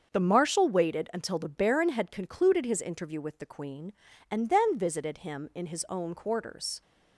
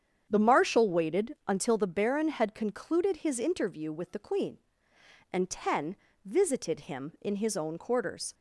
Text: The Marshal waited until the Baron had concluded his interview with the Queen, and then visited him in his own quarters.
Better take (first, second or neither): first